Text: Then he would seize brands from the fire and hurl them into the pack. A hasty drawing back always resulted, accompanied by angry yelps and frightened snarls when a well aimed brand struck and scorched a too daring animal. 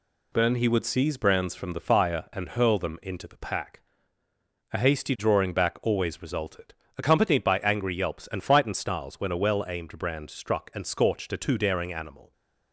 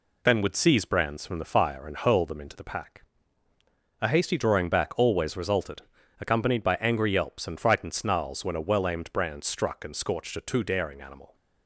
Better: first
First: none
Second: skips "he"; at 0.4 s

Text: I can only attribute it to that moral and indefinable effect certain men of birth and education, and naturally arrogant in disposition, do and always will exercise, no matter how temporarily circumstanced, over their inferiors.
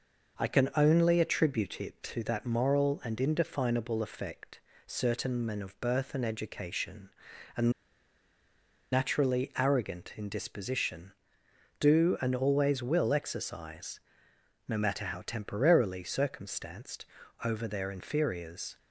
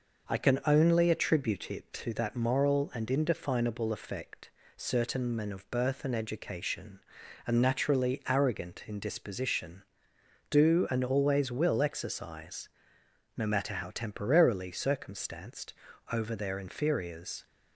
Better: second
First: pauses between "effect" and "certain"; slight; at 4.5 s; 0.26 s long // pauses between "and" and "naturally"; at 7.7 s; 1.2 s long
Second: pauses between "effect" and "certain"; slight; at 4.4 s; 0.26 s long

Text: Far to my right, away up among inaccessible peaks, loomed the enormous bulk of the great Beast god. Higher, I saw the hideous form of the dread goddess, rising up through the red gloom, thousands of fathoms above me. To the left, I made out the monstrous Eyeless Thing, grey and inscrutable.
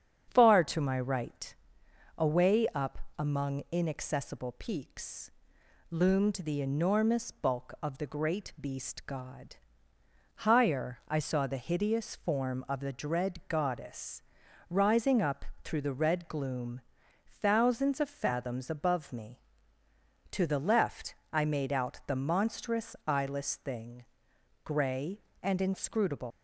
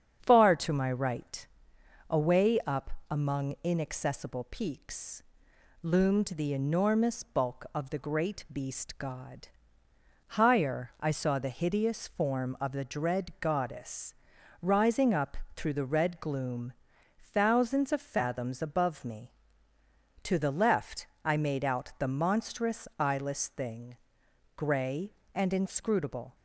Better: second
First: starts louder than the rest; strong; until 1.3 s; 7.5 dB // pauses between "up" and "among"; slight; at 2.9 s; 0.18 s long // pauses between "up" and "through"; slight; at 15.4 s; 0.18 s long // leaves "inscrutable" unfinished; at 26.3 s; 125 ms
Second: starts louder than the rest; strong; until 1.2 s; 7.5 dB // pauses between "up" and "among"; slight; at 2.9 s; 0.18 s long // pauses between "up" and "through"; slight; at 15.3 s; 0.18 s long

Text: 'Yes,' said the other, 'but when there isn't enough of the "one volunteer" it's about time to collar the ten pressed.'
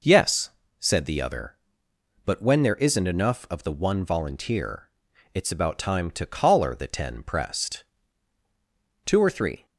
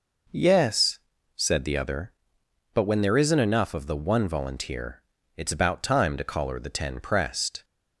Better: second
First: pauses between "volunteer" and "it's"; at 4.8 s; 0.44 s long // goes on to say "Two or three"; from 9.0 s on; 0.60 s long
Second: pauses between "volunteer" and "it's"; slight; at 5.0 s; 0.36 s long

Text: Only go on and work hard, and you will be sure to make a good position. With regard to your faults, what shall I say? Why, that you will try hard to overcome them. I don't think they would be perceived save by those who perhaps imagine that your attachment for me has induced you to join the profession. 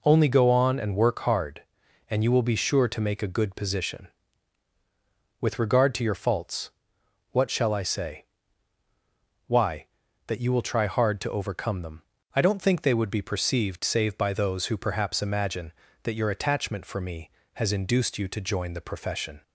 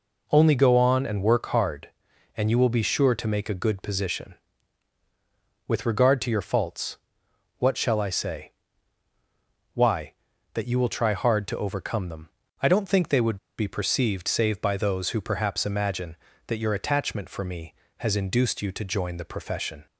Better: first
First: none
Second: pauses between "would" and "be"; slight; at 13.3 s; 0.21 s long

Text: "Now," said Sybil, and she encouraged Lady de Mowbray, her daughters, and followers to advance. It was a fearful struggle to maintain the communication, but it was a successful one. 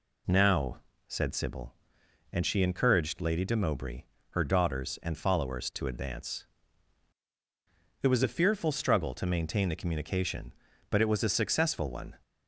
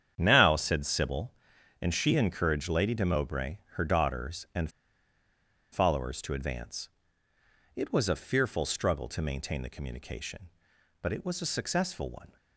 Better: first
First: none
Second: starts louder than the rest; strong; until 1.1 s; 9 dB // pauses between "and" and "followers"; at 4.7 s; 1.0 s long

